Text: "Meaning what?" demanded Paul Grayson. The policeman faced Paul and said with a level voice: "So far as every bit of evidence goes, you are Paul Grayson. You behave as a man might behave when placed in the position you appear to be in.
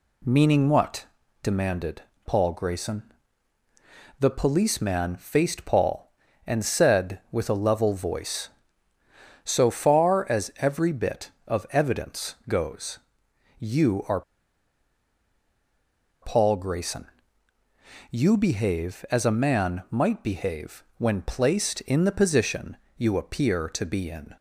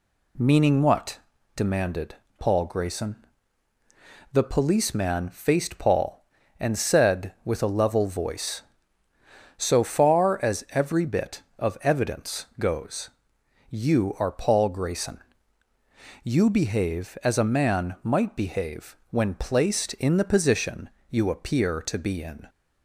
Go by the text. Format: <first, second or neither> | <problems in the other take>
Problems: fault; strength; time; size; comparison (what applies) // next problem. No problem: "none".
second | pauses between "demanded" and "Paul"; slight; at 2.0 s; 0.22 s long; slight in the second // pauses between "are" and "Paul"; strong; at 14.2 s; 2.0 s long // pauses between "behave" and "when"; slight; at 20.8 s; 0.16 s long; slight in the second // pauses between "position" and "you"; slight; at 22.7 s; 0.20 s long; slight in the second